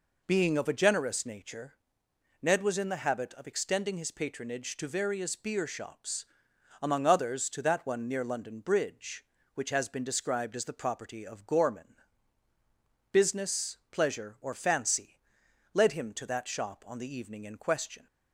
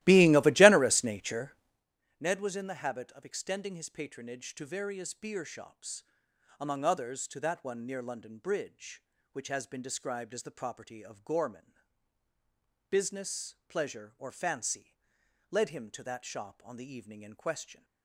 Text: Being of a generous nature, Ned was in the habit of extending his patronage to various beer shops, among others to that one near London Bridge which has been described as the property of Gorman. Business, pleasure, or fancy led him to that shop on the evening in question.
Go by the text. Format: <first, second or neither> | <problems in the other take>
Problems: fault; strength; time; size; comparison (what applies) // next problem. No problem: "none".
first | starts louder than the rest; strong; until 1.9 s; 16 dB // pauses between "fancy" and "led"; noticeable; at 14.9 s; 0.54 s long; noticeable in the first